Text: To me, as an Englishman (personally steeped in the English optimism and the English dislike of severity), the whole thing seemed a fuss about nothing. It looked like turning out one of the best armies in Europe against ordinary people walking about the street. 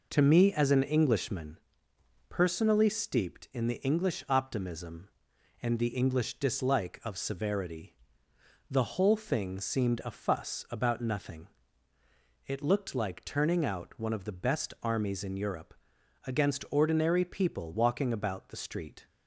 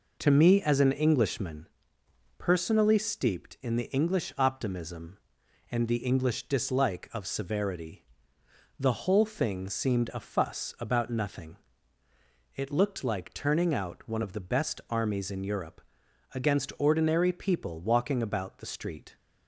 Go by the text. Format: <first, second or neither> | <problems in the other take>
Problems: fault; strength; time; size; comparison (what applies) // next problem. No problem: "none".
neither | pauses between "Europe" and "against"; noticeable; the same in both